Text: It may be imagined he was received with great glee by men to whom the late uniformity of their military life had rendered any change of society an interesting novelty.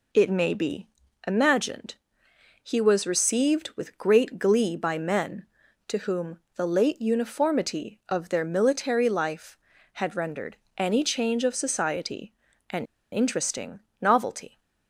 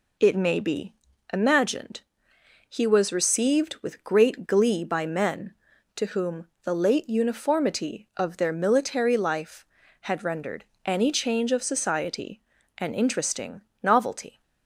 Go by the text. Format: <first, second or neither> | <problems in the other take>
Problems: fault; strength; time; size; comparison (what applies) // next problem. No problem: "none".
second | pauses between "be" and "imagined"; at 0.8 s; 0.38 s long; also in the second // pauses between "imagined" and "he"; noticeable; at 1.9 s; 0.68 s long; noticeable in the second // pauses between "whom" and "the"; slight; at 6.3 s; 0.16 s long; slight in the second // pauses between "rendered" and "any"; slight; at 10.5 s; 0.20 s long; slight in the second // pauses between "society" and "an"; slight; at 12.3 s; 0.36 s long; slight in the second // pauses between "an" and "interesting"; slight; at 12.8 s; 0.26 s long // pauses between "interesting" and "novelty"; slight; at 13.7 s; 0.20 s long; slight in the second